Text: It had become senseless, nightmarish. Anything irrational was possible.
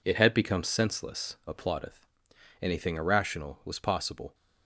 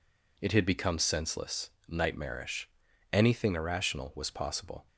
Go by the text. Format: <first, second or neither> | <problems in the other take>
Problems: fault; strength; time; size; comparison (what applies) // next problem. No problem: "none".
second | says "applaudeth" for "nightmarish"; at 1.4 s